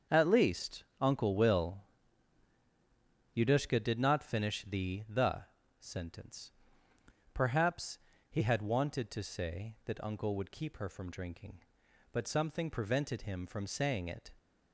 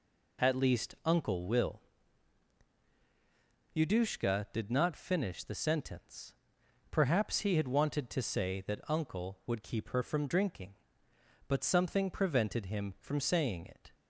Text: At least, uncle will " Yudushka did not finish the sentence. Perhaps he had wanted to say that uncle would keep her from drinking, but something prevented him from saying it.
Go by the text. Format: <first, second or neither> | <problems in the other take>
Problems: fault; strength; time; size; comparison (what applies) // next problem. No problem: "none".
second | says "the" twice; at 5.0 s // pauses between "Perhaps" and "he"; slight; at 7.9 s; 0.32 s long